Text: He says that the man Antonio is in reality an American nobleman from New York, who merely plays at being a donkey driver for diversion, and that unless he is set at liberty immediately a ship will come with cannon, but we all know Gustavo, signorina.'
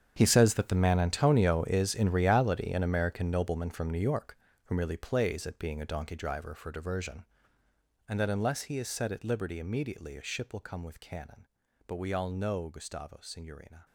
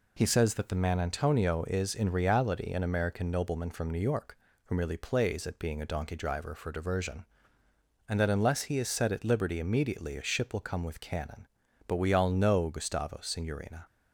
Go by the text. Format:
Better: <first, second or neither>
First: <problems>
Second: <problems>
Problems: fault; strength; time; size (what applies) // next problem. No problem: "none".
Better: second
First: gets quieter; strong; throughout; 16 dB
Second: none